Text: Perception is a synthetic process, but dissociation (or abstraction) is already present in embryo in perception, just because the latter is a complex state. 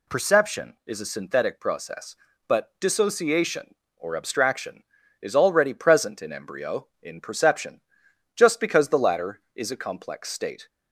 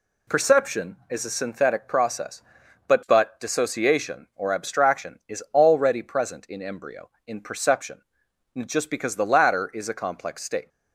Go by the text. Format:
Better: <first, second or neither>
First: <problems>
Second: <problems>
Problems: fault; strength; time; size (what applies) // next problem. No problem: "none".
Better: first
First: none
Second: says "but" twice; at 3.0 s